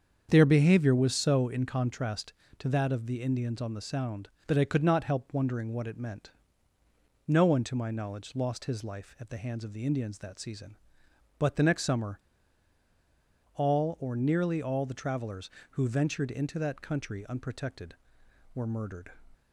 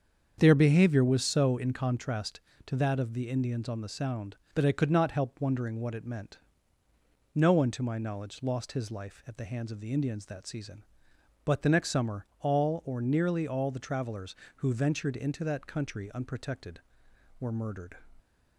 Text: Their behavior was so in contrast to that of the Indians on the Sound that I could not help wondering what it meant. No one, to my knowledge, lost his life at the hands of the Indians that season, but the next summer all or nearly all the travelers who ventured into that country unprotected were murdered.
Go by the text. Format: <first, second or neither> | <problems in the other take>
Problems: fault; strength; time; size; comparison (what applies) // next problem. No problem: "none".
second | starts louder than the rest; strong; until 1.3 s; 7 dB; strong in the second // pauses between "summer" and "all"; strong; at 12.1 s; 1.3 s long